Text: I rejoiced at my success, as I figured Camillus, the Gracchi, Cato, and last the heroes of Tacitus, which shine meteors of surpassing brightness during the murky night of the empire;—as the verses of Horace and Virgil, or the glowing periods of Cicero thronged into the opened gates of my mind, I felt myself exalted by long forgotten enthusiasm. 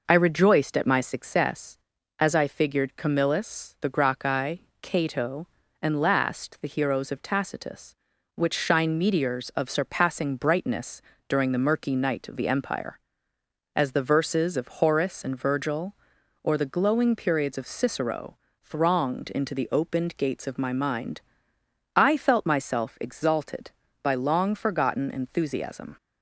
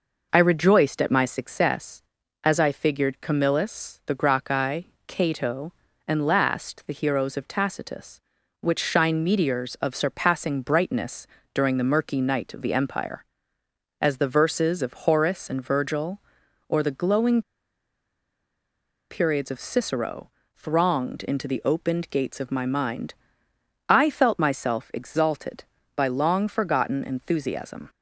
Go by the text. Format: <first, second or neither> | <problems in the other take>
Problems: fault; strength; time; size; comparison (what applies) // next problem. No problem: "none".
first | pauses between "brightness" and "during"; slight; at 11.2 s; 0.26 s long; slight in the first // pauses between "glowing" and "periods"; strong; at 17.4 s; 1.6 s long // pauses between "Cicero" and "thronged"; slight; at 20.2 s; 0.26 s long; slight in the first